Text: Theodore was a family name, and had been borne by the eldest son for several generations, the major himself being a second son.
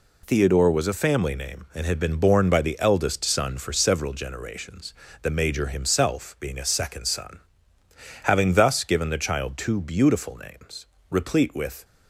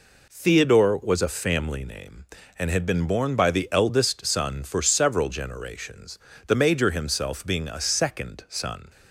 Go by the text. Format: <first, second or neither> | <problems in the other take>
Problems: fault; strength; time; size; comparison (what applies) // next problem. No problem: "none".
second | goes on to say "Having thus given the child two beautiful names replete with"; strong; from 8.2 s on; 3.6 s long